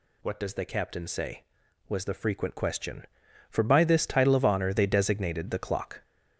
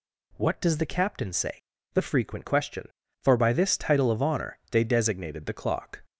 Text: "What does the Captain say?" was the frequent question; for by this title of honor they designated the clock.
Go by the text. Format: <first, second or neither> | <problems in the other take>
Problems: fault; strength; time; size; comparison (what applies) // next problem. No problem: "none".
first | skips "was"; at 1.7 s